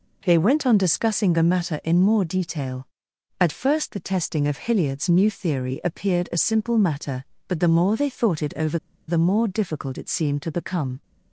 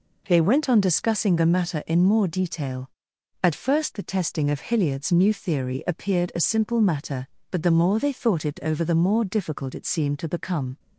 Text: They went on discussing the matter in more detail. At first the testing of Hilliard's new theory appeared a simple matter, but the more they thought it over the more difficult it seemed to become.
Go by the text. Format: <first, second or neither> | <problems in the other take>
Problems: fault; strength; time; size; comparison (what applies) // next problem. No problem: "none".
second | pauses between "over" and "the"; slight; at 8.7 s; 0.31 s long